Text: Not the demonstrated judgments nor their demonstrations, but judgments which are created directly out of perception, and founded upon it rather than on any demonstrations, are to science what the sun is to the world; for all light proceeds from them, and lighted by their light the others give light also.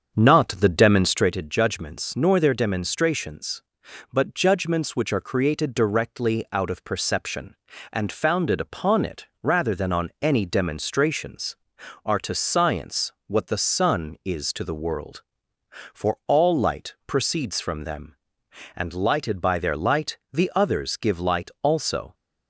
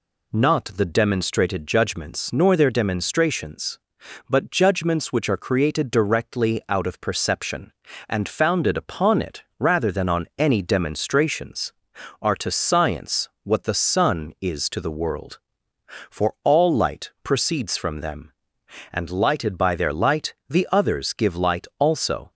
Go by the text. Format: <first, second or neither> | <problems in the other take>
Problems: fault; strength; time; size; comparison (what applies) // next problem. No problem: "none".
second | starts louder than the rest; until 1.3 s; 7 dB // pauses between "it" and "rather"; slight; at 9.2 s; 0.16 s long; slight in the second